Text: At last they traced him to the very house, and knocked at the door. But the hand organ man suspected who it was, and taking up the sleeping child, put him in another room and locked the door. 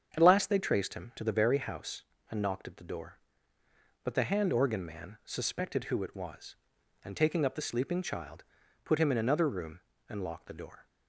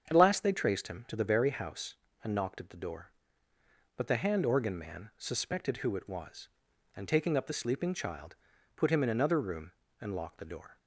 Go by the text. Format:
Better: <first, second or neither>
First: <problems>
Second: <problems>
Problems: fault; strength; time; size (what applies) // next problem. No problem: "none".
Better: neither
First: starts louder than the rest; strong; until 1.1 s; 7.5 dB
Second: starts louder than the rest; strong; until 1.1 s; 7.5 dB